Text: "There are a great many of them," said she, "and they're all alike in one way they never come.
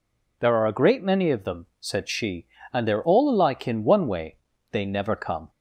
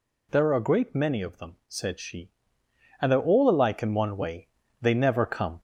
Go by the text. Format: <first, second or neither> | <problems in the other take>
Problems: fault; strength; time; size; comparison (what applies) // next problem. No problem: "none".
first | gets louder; slight; throughout; 3 dB // pauses between "way" and "they"; slight; at 4.4 s; 0.34 s long; slight in the first